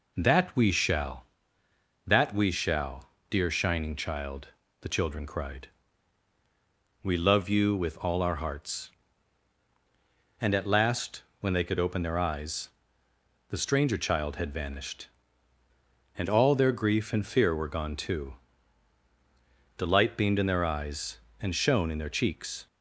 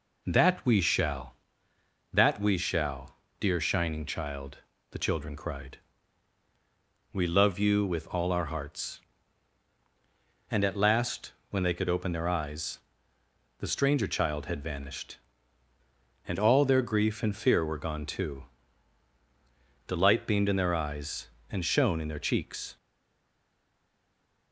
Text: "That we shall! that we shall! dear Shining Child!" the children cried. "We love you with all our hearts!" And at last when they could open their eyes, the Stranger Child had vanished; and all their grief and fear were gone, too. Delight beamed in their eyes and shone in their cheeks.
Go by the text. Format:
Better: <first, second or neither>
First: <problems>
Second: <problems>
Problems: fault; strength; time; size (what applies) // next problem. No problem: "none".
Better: first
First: pauses between "last" and "when"; slight; at 11.2 s; 0.18 s long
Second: pauses between "last" and "when"; slight; at 11.3 s; 0.18 s long // stays silent after the last word; noticeable; from 22.7 s on; 1.8 s long